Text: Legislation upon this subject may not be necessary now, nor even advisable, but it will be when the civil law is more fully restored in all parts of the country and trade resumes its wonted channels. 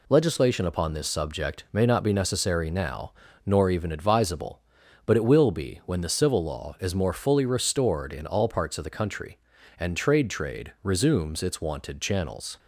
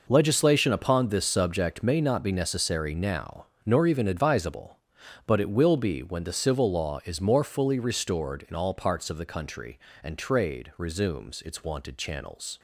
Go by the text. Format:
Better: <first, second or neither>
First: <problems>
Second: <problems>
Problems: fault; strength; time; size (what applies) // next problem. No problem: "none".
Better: second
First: says "trade" twice; at 10.3 s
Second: none